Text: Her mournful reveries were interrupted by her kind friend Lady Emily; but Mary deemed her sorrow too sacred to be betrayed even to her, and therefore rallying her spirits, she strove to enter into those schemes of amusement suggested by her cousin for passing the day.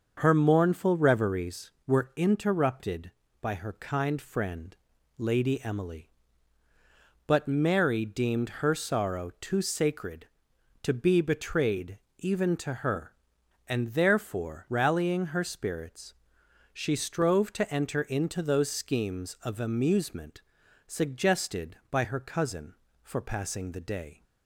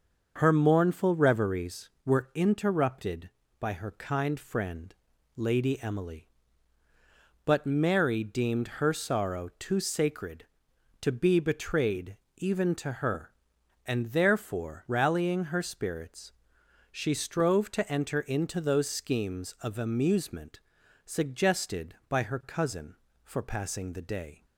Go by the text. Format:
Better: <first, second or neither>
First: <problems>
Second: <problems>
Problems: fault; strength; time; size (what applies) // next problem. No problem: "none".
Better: neither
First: starts louder than the rest; until 1.1 s; 6.5 dB // pauses between "friend" and "Lady"; at 4.7 s; 0.42 s long // pauses between "betrayed" and "even"; slight; at 12.0 s; 0.18 s long // pauses between "amusement" and "suggested"; noticeable; at 20.4 s; 0.46 s long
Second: starts louder than the rest; until 1.3 s; 6.5 dB // pauses between "friend" and "Lady"; at 4.9 s; 0.42 s long // pauses between "betrayed" and "even"; slight; at 12.1 s; 0.18 s long // pauses between "amusement" and "suggested"; noticeable; at 20.6 s; 0.46 s long